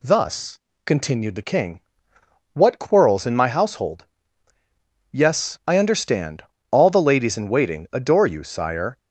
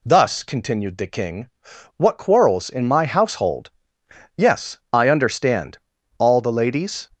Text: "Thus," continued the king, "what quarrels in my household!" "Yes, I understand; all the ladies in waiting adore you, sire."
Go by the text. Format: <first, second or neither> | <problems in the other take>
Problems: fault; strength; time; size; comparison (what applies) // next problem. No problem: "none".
first | stops before "in waiting adore you sire"; at 7.1 s